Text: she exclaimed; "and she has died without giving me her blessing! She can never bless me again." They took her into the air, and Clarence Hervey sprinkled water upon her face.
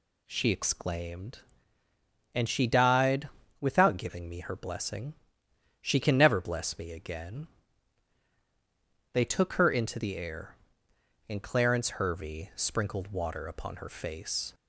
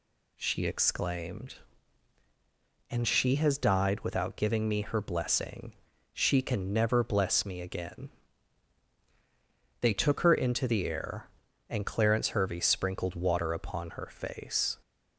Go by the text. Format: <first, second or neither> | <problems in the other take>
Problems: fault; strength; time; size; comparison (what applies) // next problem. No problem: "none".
second | skips "has"; at 2.6 s // pauses between "died" and "without"; slight; at 3.2 s; 0.30 s long